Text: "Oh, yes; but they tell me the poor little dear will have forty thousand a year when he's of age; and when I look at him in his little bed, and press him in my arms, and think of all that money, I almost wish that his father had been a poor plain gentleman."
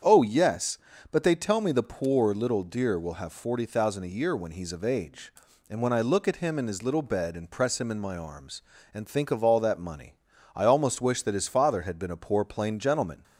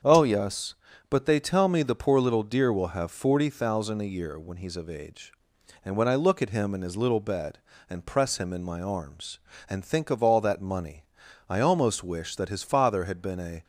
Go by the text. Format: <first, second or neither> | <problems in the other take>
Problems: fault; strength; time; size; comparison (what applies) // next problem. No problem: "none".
first | starts louder than the rest; strong; until 1.4 s; 7.5 dB; strong in the first // stops before "poor plain gentleman"; at 13.6 s